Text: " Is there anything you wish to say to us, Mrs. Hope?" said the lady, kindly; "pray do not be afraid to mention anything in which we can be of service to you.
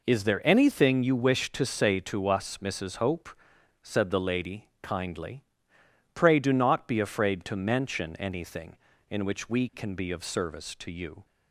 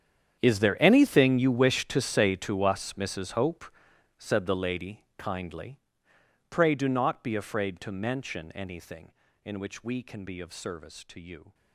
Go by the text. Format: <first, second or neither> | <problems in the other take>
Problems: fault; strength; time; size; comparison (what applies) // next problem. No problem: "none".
first | gets quieter; strong; throughout; 18.5 dB